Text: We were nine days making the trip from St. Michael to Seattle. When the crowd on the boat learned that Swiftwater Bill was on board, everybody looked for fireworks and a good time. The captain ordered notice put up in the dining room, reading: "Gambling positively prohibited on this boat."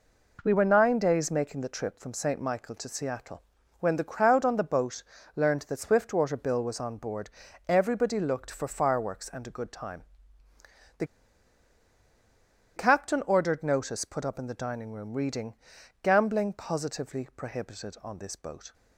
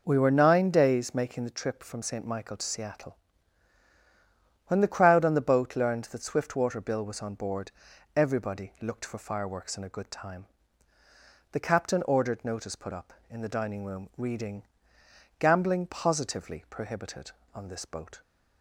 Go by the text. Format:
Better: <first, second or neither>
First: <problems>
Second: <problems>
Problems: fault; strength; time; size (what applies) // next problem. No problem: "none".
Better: second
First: pauses between "boat" and "learned"; slight; at 5.0 s; 0.34 s long // pauses between "The" and "captain"; strong; at 11.0 s; 1.7 s long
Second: none